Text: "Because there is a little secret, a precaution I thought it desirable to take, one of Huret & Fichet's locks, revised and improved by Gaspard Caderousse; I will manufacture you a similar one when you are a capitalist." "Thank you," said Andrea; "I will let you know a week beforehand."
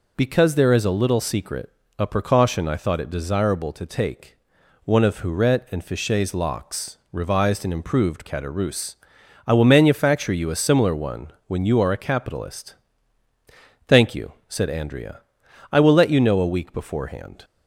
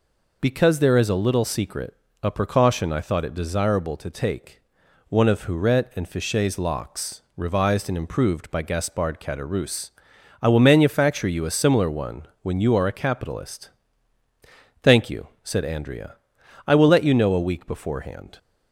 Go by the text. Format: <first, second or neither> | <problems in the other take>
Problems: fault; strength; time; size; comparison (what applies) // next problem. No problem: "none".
second | skips "by Gaspard"; at 8.2 s // pauses between "one" and "when"; slight; at 11.3 s; 0.16 s long; slight in the second